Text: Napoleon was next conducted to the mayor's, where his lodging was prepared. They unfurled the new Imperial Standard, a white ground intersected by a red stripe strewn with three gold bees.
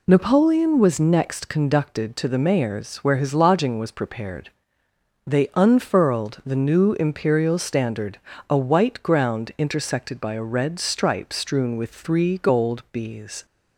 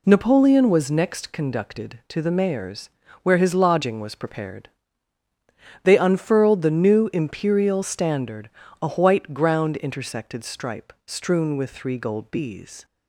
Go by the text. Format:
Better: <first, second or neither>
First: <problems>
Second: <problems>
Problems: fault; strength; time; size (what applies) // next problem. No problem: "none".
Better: first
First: none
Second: skips "by a red"; at 10.4 s